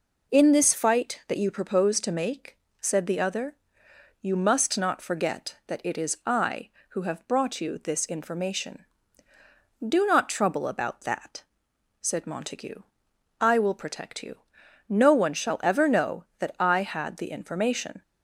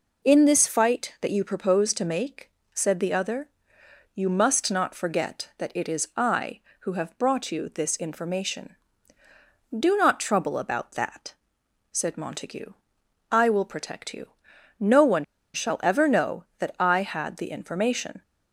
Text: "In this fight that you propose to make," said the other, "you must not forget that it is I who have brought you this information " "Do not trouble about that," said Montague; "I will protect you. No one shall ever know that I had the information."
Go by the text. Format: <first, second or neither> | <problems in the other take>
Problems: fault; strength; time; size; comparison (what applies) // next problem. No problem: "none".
first | pauses between "one" and "shall"; slight; at 15.2 s; 0.29 s long